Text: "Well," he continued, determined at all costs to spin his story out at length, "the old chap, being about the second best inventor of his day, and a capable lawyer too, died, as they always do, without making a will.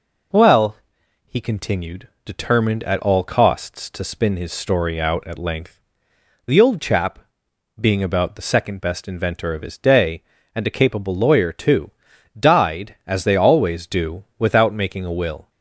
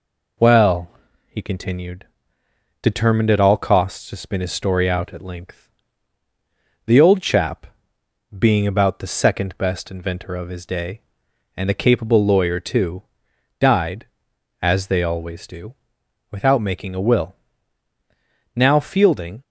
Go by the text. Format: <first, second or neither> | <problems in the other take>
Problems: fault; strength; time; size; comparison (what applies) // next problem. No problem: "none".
first | goes on to say "Now Fielding"; noticeable; from 18.5 s on; 0.86 s long